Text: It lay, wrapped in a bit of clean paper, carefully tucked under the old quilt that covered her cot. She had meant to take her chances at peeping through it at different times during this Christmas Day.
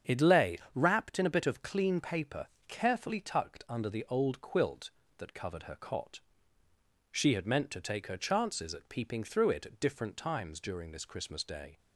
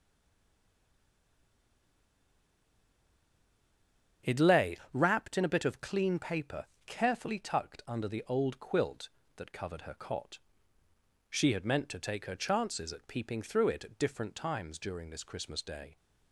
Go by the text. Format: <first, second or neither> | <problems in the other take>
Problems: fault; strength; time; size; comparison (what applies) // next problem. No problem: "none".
first | stays silent before the first word; strong; until 4.2 s; 4.2 s long // starts louder than the rest; strong; until 5.4 s; 8 dB; strong in the first